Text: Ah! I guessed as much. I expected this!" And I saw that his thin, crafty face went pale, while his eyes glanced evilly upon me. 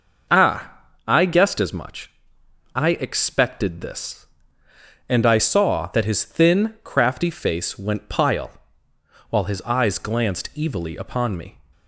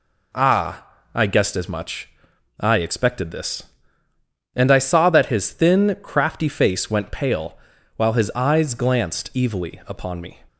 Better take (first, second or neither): second